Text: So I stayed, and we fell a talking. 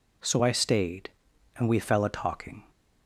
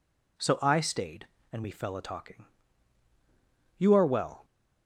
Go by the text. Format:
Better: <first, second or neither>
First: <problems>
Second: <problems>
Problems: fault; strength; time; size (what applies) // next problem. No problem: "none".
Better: first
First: none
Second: goes on to say "You are well"; noticeable; from 3.7 s on; 0.68 s long